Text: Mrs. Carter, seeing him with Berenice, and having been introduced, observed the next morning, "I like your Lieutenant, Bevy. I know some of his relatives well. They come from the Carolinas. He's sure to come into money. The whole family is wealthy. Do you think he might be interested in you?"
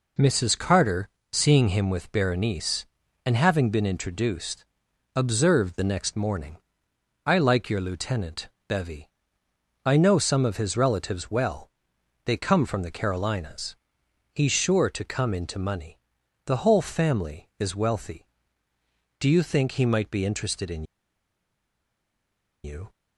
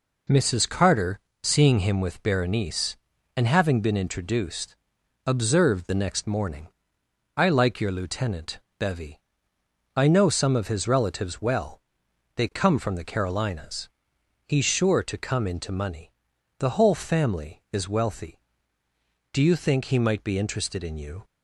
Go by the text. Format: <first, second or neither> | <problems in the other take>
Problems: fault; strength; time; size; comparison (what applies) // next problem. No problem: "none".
second | pauses between "in" and "you"; strong; at 20.8 s; 1.8 s long